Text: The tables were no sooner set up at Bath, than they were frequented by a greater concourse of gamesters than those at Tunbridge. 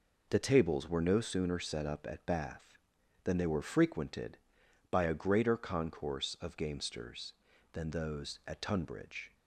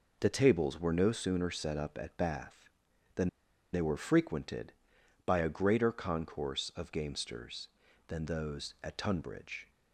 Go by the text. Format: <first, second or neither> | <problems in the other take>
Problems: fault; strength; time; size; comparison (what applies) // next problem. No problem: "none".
first | pauses between "than" and "they"; at 3.2 s; 0.44 s long